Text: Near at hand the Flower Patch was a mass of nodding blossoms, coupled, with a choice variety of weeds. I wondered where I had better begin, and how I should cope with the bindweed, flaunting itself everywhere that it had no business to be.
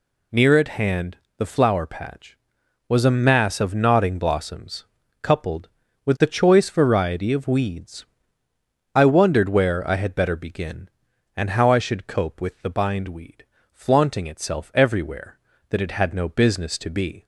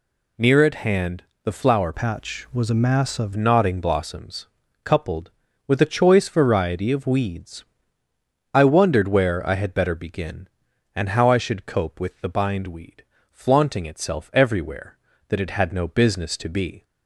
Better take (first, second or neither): first